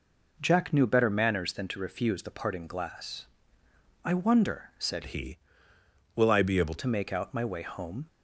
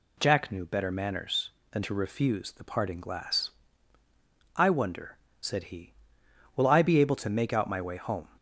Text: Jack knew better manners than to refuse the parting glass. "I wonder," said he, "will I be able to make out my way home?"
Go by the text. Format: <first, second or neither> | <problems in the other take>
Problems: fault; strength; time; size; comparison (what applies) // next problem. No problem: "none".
second | changes voice from "he" to "able"; from 5.0 to 6.7 s; 1.7 s long